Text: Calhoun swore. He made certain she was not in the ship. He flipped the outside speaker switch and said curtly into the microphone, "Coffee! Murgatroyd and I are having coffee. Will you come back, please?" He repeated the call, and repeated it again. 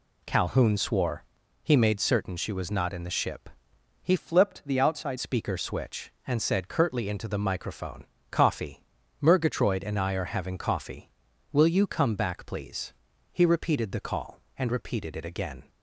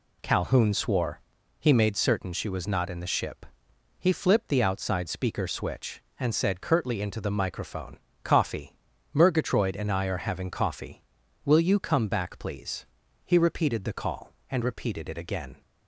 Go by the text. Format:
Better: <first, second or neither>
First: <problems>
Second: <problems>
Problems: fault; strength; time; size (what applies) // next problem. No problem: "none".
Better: second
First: changes voice from "flipped" to "outside"; from 4.1 to 5.1 s; 1.0 s long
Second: none